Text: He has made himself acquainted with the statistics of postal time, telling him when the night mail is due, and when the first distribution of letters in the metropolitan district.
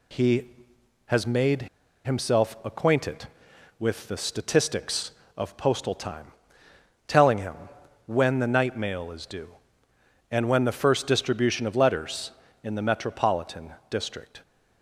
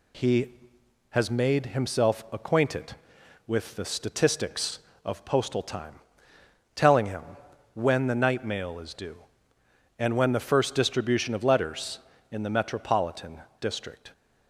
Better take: second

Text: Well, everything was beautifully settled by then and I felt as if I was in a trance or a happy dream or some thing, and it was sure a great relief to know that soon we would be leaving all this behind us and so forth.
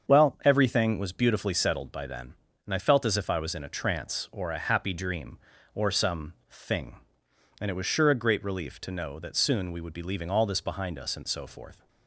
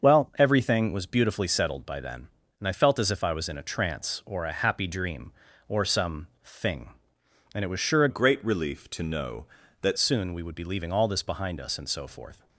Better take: first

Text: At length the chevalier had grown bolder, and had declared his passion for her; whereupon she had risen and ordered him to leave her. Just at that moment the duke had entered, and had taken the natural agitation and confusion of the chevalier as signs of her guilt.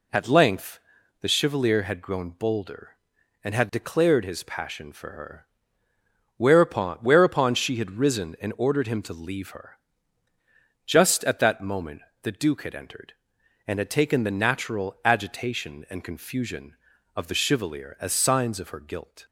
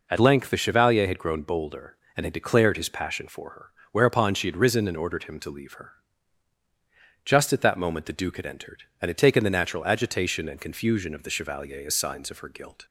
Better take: second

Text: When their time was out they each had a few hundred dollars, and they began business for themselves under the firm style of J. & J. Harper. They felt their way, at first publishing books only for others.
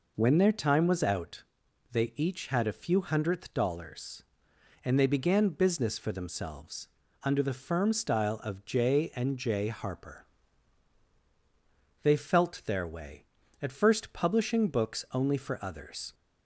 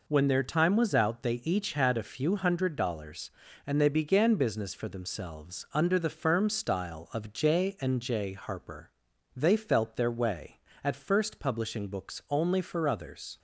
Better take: second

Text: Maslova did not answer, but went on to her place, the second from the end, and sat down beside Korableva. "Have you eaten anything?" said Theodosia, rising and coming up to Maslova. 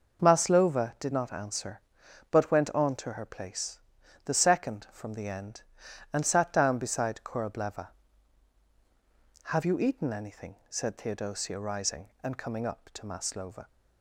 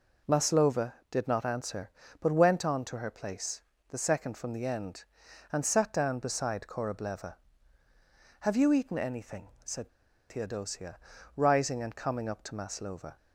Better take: first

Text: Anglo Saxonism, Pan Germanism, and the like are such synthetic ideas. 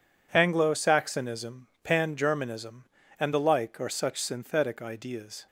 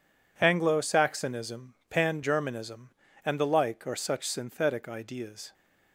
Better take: neither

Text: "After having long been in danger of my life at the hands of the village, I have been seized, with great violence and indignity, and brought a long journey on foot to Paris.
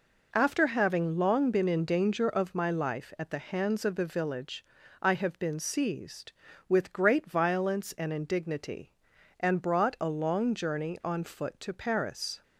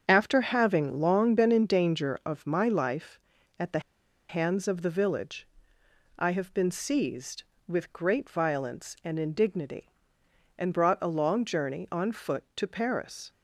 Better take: first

